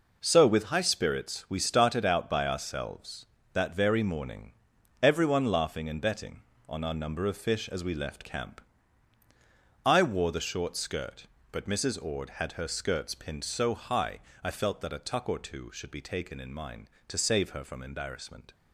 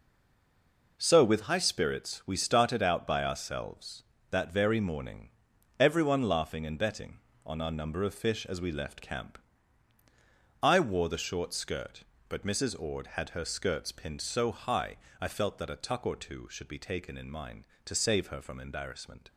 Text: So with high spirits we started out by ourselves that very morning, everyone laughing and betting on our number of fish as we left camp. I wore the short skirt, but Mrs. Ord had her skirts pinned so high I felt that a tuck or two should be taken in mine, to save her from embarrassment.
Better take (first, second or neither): first